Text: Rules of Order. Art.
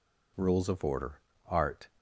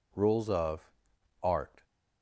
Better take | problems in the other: first | skips "Order"; at 1.1 s

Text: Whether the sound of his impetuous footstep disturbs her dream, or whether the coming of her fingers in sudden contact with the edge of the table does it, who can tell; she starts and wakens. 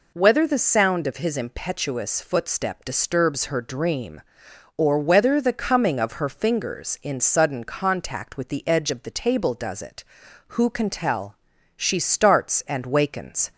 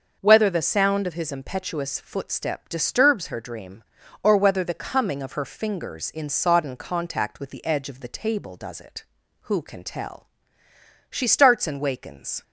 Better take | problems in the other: first | starts louder than the rest; until 1.2 s; 6.5 dB // says "sodden" for "sudden"; at 6.2 s

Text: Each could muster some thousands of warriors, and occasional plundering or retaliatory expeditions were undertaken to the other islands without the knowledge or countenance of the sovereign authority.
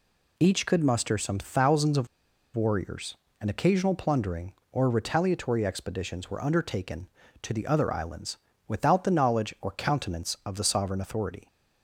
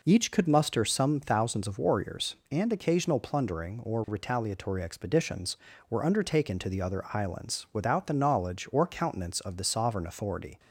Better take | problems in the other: second | pauses between "of" and "warriors"; noticeable; at 2.0 s; 0.49 s long // pauses between "islands" and "without"; slight; at 8.3 s; 0.30 s long

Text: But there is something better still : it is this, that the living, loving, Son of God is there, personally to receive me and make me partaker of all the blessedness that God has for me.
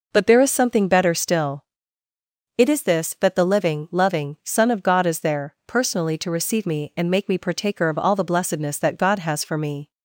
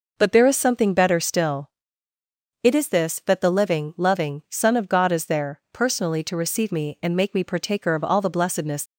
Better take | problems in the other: first | stops before "that God has for me"; at 8.8 s

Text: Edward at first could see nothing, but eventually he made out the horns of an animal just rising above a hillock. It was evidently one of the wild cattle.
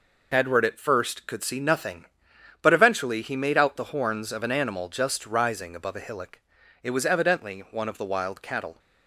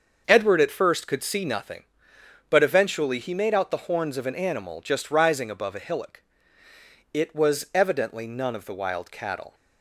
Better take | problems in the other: first | starts louder than the rest; until 1.2 s; 6.5 dB // says "none" for "one"; at 8.2 s

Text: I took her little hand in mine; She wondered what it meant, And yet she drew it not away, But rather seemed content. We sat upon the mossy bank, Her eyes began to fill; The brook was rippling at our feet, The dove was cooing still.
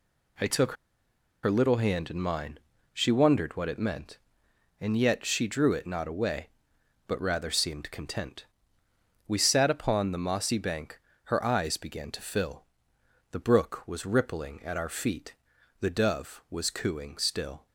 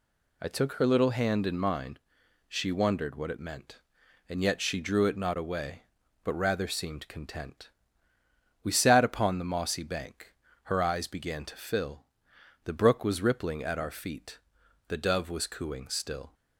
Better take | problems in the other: second | pauses between "took" and "her"; noticeable; at 0.7 s; 0.70 s long

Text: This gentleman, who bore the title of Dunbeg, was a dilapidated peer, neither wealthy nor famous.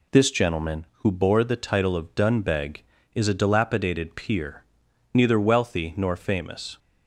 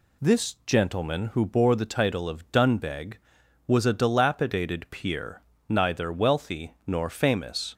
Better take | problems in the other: second | says "is" for "was"; at 3.1 s

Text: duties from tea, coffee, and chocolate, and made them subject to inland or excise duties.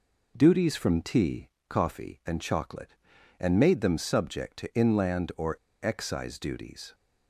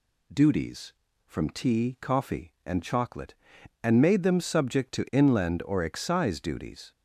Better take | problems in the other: second | pauses between "or" and "excise"; slight; at 5.5 s; 0.27 s long

